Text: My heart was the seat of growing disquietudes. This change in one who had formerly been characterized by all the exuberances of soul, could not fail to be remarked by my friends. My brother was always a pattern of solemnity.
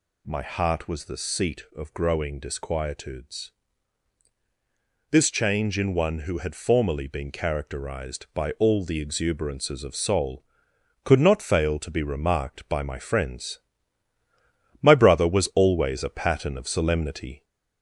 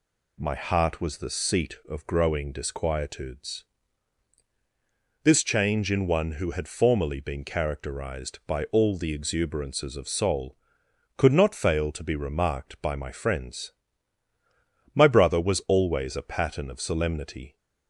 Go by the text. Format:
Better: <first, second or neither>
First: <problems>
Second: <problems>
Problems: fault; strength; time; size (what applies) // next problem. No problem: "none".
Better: second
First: gets louder; slight; throughout; 3 dB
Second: none